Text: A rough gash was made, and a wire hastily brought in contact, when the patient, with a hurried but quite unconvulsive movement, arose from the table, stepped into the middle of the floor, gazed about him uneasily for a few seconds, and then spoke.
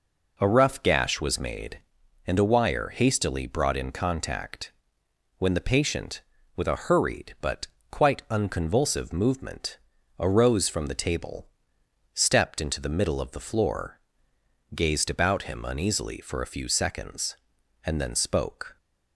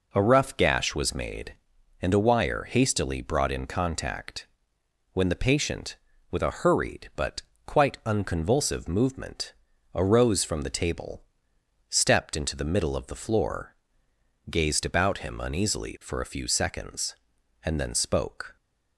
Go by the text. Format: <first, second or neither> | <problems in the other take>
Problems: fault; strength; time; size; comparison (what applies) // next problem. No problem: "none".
neither | pauses between "but" and "quite"; slight; the same in both